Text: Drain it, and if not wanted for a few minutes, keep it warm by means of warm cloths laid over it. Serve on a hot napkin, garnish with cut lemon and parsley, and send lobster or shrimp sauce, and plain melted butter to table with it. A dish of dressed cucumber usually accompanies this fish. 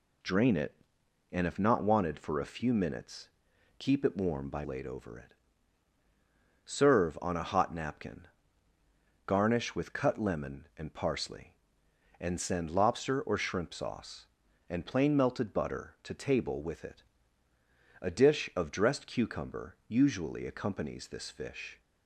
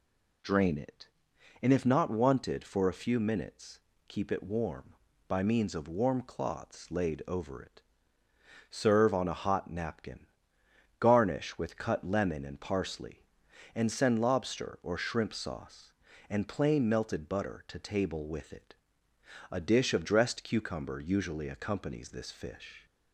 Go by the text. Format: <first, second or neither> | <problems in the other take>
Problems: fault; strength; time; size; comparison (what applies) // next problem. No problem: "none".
second | skips "means of warm cloths"; at 4.6 s